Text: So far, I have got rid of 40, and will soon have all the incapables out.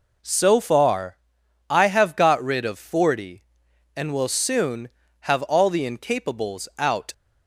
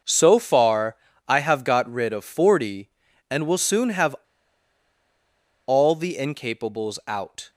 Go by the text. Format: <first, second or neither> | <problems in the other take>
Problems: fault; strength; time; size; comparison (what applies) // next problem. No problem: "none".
first | starts louder than the rest; noticeable; until 1.3 s; 6 dB // pauses between "have" and "all"; strong; at 4.1 s; 1.5 s long